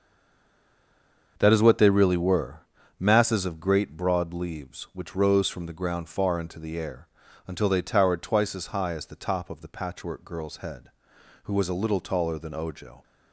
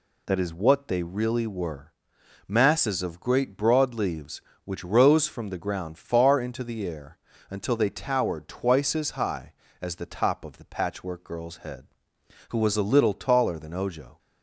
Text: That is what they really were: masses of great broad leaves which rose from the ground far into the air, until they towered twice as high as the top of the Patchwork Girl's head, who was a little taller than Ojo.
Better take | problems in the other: second | stays silent before the first word; noticeable; until 1.3 s; 1.3 s long // starts louder than the rest; until 2.3 s; 6.5 dB

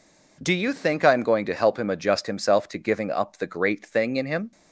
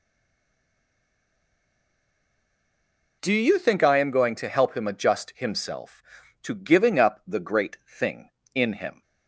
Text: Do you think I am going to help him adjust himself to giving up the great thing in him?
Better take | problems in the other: first | stays silent before the first word; strong; until 3.2 s; 3.2 s long

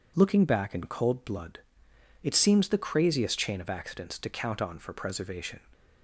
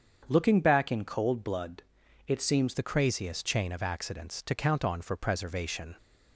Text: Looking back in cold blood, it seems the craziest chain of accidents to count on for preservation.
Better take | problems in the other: first | starts louder than the rest; strong; until 1.3 s; 7 dB // changes voice at "the"; from 2.7 s on; 3.2 s long

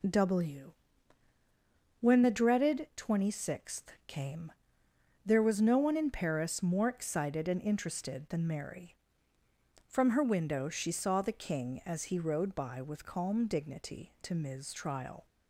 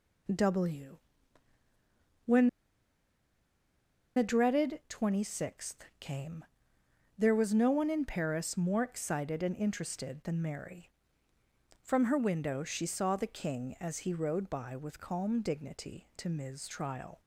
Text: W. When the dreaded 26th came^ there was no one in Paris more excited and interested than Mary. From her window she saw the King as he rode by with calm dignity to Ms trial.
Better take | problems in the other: first | pauses between "When" and "the"; strong; at 2.4 s; 1.6 s long // pauses between "came" and "there"; noticeable; at 6.4 s; 0.72 s long; noticeable in the first

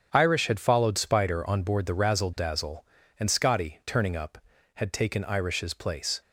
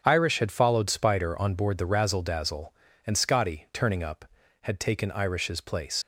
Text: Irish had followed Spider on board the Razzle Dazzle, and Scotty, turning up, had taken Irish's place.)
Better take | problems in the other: first | starts louder than the rest; strong; until 1.0 s; 8 dB; strong in the first // leaves "place" unfinished; at 6.0 s; 55 ms

